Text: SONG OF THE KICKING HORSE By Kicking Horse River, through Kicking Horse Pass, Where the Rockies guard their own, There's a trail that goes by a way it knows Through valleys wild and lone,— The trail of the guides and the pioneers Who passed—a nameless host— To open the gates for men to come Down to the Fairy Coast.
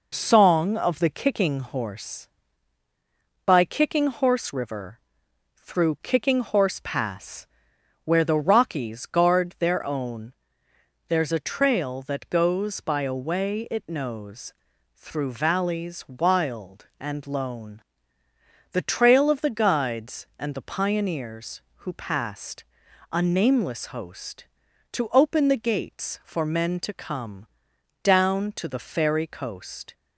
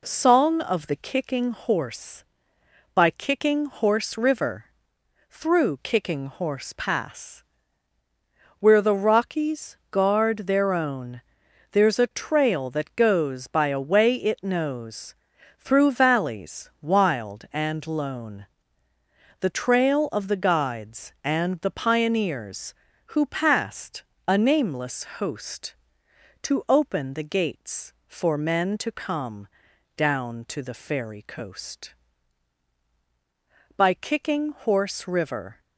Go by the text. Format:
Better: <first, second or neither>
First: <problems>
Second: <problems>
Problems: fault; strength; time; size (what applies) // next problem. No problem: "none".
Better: first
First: pauses between "knows" and "Through"; at 14.5 s; 0.42 s long // pauses between "come" and "Down"; noticeable; at 27.4 s; 0.54 s long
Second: pauses between "knows" and "Through"; at 15.1 s; 0.42 s long // pauses between "nameless" and "host"; slight; at 25.0 s; 0.16 s long // pauses between "come" and "Down"; noticeable; at 29.4 s; 0.48 s long // goes on to say "By Kicking Horse River"; strong; from 33.7 s on; 1.8 s long